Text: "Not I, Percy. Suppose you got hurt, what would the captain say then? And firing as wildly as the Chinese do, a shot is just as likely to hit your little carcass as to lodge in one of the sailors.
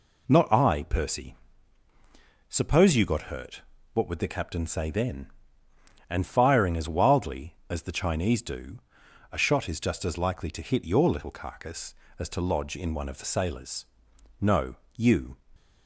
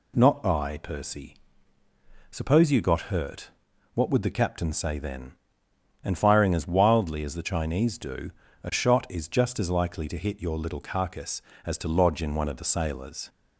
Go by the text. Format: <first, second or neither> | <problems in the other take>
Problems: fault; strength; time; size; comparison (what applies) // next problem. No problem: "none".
second | goes on to say "No you"; noticeable; from 14.4 s on; 0.96 s long